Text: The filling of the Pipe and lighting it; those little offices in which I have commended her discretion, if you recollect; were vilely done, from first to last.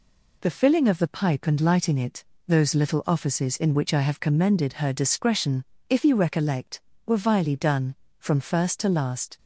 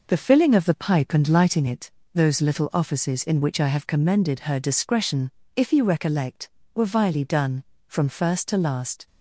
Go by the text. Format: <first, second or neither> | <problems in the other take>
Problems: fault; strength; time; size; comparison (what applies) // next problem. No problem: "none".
first | starts louder than the rest; noticeable; until 1.7 s; 5 dB